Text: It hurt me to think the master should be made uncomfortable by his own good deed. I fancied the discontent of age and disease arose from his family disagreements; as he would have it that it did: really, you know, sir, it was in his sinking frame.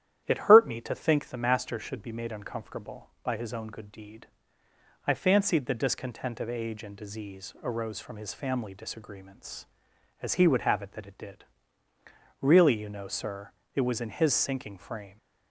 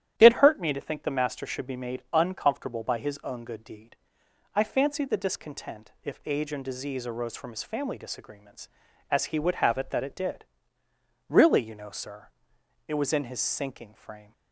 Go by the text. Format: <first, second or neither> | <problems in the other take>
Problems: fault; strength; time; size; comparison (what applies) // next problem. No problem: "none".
first | starts louder than the rest; strong; until 1.1 s; 11 dB; strong in the first // says "if" for "of"; at 6.0 s